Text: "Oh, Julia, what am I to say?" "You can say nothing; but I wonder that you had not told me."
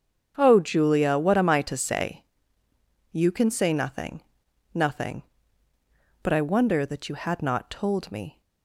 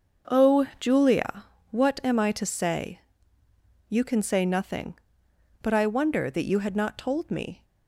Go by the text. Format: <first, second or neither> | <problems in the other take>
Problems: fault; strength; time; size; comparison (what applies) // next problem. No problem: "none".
second | starts louder than the rest; strong; until 1.3 s; 7 dB; also in the second // says "nothing" twice; at 4.7 s